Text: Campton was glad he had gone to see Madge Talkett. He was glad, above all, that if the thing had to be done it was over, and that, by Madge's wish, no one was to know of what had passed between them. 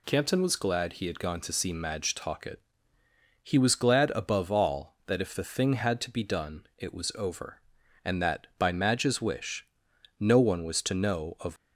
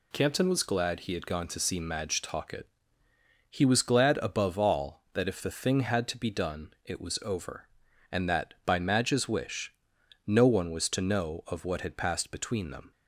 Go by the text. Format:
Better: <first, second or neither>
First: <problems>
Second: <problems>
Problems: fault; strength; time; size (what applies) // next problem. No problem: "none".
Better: second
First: stops before "what had passed between them"; at 11.5 s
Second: none